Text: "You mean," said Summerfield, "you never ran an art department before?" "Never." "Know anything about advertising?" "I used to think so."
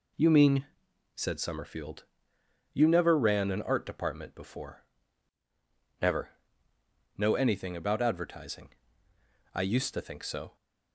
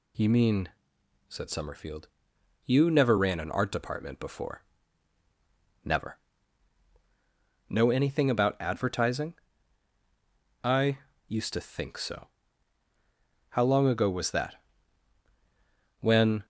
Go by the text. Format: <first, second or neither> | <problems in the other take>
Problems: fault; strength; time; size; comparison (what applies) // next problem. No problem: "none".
first | pauses between "I" and "used"; slight; at 10.9 s; 0.28 s long // goes on to say "How long ago was that When"; strong; from 13.4 s on; 2.9 s long